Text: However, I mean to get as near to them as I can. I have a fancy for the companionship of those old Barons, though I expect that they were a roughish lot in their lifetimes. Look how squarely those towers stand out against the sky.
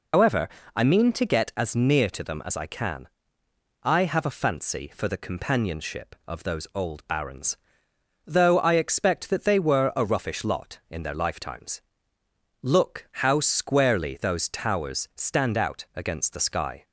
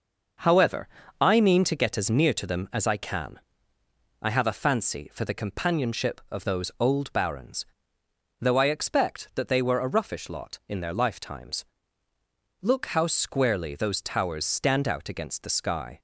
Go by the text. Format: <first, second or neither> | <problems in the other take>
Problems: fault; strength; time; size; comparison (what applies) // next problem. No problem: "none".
second | loses the start of "However"; at 0.1 s; 115 ms